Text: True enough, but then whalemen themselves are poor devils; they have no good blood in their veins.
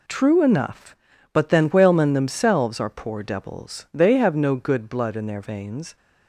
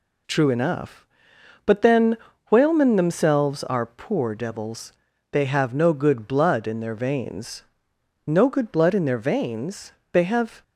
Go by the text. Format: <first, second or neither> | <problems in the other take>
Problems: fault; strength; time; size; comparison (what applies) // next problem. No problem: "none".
first | pauses between "then" and "whalemen"; slight; at 2.1 s; 0.34 s long // goes on to say "No good blood in their veins They have"; strong; from 8.2 s on; 2.3 s long